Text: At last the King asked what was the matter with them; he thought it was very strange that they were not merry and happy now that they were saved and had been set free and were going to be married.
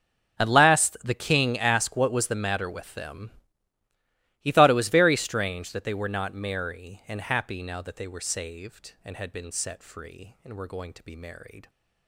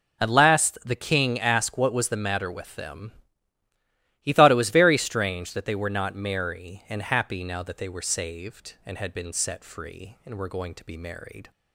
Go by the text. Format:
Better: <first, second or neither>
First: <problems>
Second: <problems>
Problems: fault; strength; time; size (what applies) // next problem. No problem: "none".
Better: second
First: gets quieter; strong; throughout; 20 dB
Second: none